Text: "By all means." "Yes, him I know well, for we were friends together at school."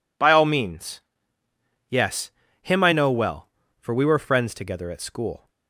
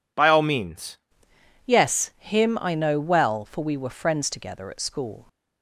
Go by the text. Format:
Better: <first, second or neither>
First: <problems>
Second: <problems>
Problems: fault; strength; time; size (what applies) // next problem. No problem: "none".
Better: first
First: none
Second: changes voice at "Yes"; from 1.6 s on; 3.6 s long